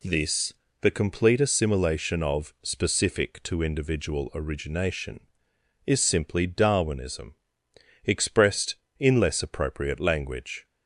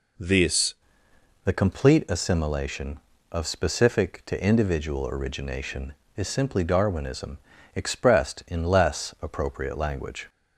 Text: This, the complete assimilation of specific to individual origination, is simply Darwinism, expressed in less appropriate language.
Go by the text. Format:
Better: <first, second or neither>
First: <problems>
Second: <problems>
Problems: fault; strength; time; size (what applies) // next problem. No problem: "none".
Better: first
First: none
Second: changes voice at "the"; from 1.4 s on; 8.8 s long